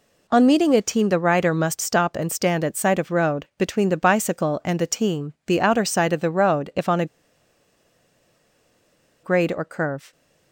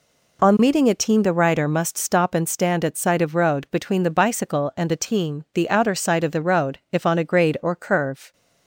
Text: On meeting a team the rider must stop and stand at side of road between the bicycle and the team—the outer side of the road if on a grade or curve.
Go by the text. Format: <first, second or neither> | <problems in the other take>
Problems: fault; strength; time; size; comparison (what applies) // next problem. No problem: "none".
second | pauses between "a" and "grade"; strong; at 7.0 s; 2.1 s long